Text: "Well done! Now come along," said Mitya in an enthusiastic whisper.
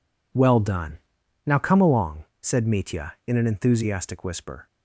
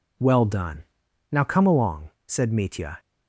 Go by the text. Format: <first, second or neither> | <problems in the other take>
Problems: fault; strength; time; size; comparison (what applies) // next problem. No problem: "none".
first | stops before "in an enthusiastic whisper"; at 2.9 s